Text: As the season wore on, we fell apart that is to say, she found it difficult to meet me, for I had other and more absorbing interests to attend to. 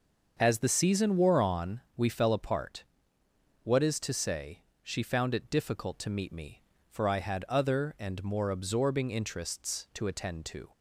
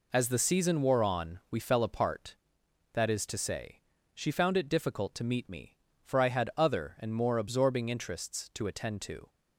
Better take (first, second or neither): second